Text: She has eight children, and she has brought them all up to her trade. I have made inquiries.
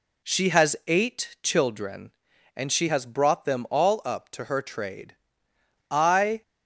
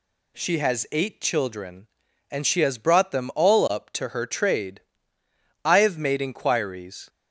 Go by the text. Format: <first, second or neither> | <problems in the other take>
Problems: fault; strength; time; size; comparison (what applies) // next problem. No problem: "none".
second | stops before "have made inquiries"; at 6.4 s